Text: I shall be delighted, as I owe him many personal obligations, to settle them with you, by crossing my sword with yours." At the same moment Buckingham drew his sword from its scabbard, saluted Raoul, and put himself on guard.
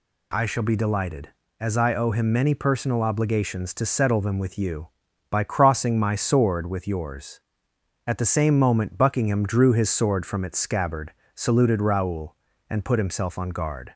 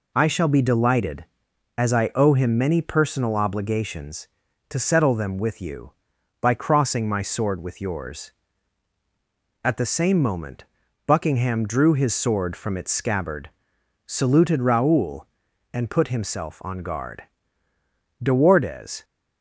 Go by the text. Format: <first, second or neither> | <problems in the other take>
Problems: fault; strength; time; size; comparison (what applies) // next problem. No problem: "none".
first | pauses between "moment" and "Buckingham"; at 10.6 s; 0.42 s long // goes on to say "De Wardes"; noticeable; from 18.2 s on; 0.82 s long